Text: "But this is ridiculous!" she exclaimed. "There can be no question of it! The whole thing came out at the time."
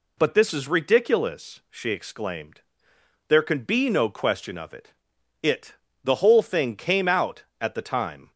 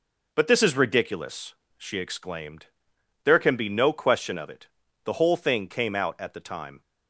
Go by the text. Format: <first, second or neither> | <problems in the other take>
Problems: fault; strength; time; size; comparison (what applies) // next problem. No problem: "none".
second | says "it" twice; at 5.4 s